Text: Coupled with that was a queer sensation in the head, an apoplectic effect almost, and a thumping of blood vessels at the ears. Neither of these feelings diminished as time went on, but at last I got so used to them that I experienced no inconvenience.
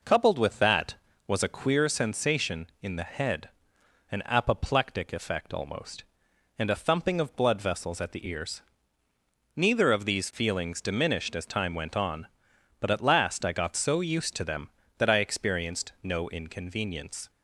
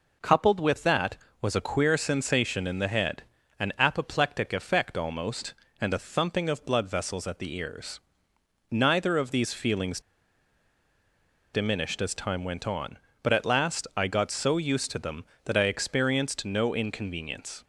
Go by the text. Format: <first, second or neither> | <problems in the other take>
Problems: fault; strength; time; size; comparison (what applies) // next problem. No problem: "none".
first | pauses between "feelings" and "diminished"; strong; at 10.0 s; 1.5 s long